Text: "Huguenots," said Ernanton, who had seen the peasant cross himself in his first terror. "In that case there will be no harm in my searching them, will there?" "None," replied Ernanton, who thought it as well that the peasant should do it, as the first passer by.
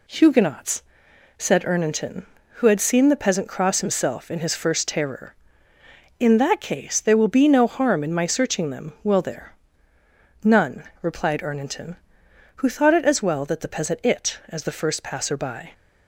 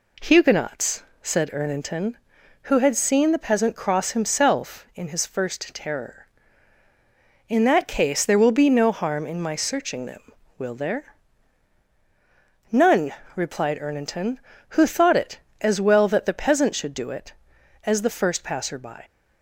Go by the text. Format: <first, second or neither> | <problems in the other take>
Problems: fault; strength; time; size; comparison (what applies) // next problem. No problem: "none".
second | skips "should do"; at 14.0 s